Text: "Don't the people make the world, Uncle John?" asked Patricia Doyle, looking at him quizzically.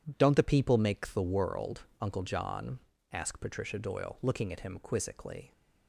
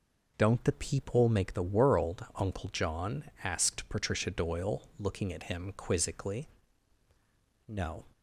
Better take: first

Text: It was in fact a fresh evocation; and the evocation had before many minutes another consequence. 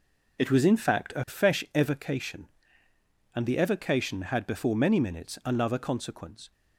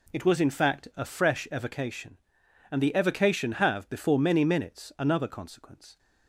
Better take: first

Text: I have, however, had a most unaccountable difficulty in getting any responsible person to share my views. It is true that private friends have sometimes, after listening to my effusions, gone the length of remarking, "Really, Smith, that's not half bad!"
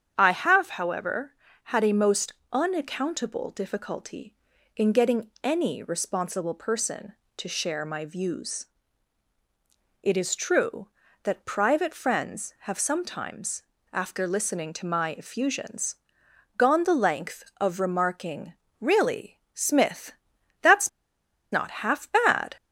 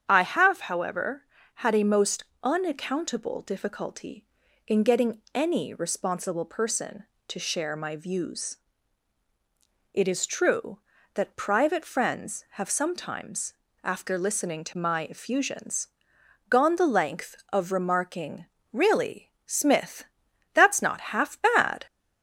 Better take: second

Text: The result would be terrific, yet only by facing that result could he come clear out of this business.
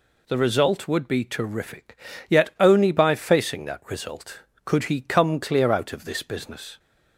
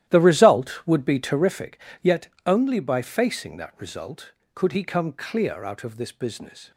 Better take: first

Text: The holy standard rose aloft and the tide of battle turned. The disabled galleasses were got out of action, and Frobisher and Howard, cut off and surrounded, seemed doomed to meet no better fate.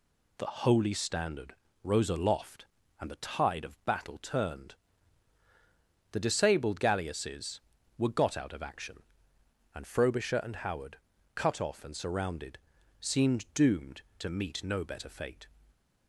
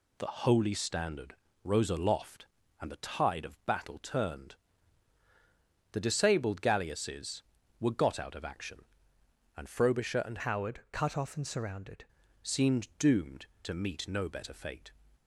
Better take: first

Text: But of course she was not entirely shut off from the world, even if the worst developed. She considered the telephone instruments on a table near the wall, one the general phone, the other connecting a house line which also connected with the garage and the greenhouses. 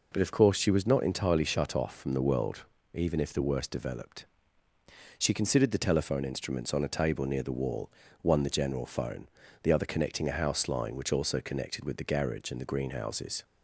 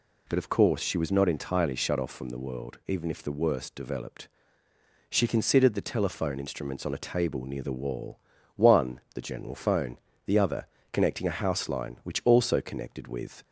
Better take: first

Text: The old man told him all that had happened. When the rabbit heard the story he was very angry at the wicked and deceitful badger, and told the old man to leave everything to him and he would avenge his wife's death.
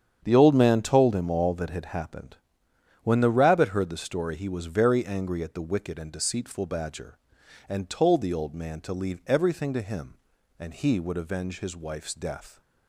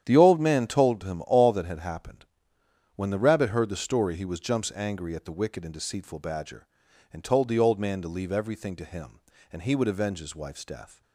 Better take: first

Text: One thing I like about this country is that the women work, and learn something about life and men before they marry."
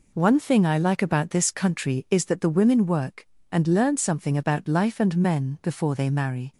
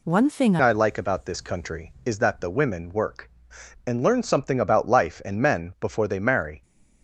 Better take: first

